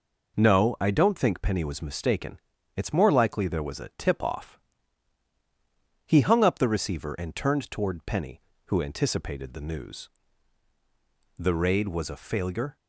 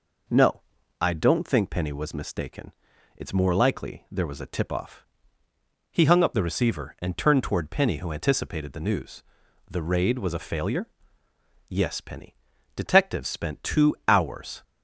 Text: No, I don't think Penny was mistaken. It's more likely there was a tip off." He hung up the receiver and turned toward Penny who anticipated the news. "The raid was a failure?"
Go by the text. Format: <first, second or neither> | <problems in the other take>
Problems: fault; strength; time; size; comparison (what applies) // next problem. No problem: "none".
first | goes on to say "Yes Penny Detectives spent two hours"; strong; from 11.6 s on; 2.9 s long